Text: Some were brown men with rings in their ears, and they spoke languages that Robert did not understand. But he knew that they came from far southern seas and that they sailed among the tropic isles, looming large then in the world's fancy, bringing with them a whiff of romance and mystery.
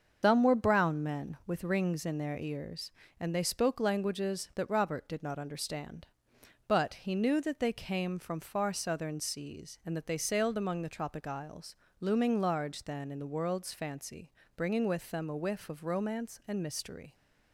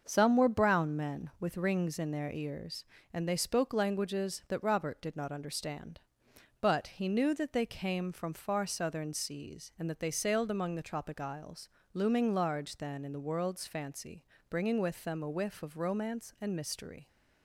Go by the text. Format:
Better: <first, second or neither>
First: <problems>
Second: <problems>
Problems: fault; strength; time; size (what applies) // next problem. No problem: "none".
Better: second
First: loses the start of "Some"; at 0.2 s; 110 ms // starts louder than the rest; until 1.2 s; 6.5 dB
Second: starts louder than the rest; until 1.0 s; 6.5 dB